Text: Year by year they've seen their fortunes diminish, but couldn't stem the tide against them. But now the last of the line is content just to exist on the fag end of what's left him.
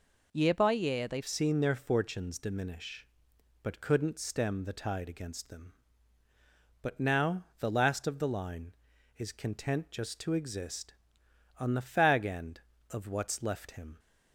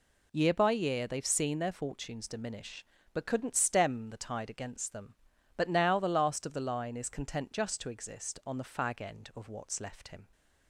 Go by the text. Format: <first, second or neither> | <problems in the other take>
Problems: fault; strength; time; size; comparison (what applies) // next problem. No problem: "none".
second | changes voice at "seen"; from 1.2 s on; 12.7 s long // pauses between "now" and "the"; slight; at 7.4 s; 0.16 s long